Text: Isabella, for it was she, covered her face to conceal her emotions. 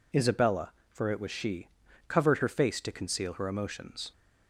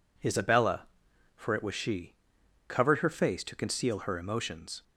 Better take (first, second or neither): neither